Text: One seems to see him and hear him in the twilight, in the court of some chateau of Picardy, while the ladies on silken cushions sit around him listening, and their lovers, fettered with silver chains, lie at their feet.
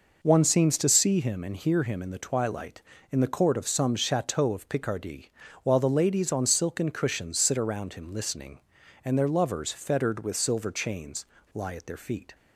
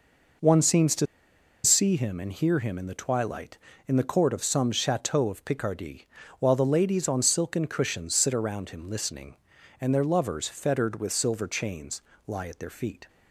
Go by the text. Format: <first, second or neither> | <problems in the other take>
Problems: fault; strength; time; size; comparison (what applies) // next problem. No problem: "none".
first | pauses between "to" and "see"; noticeable; at 1.0 s; 0.58 s long